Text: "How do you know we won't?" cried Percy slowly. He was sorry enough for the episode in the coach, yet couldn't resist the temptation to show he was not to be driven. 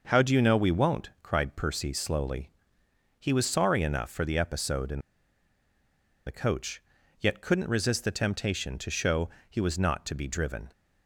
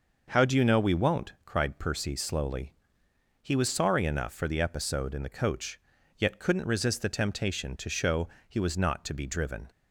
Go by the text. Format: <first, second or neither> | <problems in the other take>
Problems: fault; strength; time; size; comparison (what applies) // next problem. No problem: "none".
second | pauses between "in" and "the"; strong; at 4.9 s; 1.2 s long // pauses between "show" and "he"; slight; at 9.2 s; 0.20 s long; slight in the second